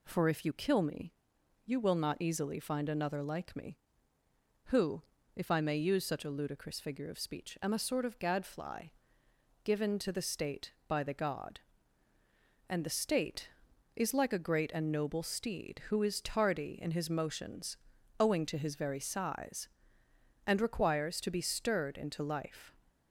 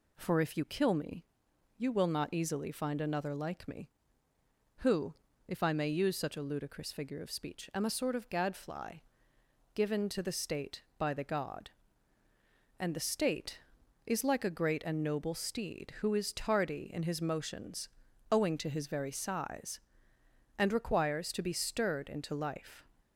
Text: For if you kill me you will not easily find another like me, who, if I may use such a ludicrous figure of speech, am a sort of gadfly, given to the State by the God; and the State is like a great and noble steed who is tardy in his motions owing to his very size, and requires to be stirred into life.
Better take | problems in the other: neither | pauses between "me" and "you"; noticeable; the same in both // pauses between "motions" and "owing"; the same in both

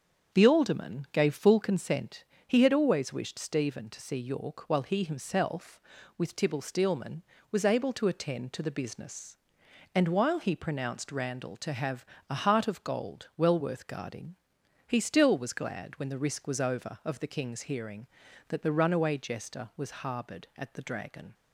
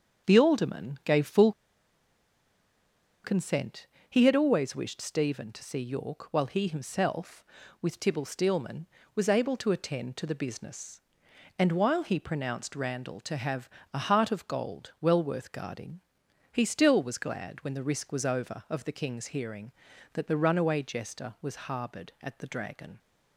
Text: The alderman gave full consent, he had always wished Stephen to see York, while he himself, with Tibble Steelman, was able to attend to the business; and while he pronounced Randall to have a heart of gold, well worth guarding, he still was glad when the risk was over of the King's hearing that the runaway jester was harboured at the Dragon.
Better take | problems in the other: first | starts louder than the rest; strong; until 1.3 s; 7 dB; strong in the first // pauses between "full" and "consent"; strong; at 1.5 s; 1.7 s long // pauses between "have" and "a"; slight; at 13.6 s; 0.24 s long; slight in the first

